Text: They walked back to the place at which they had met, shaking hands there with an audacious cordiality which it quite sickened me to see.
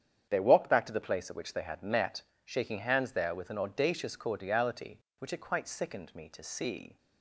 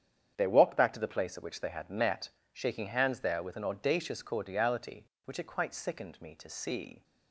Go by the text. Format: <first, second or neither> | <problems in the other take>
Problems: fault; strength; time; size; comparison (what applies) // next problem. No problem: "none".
neither | starts louder than the rest; strong; the same in both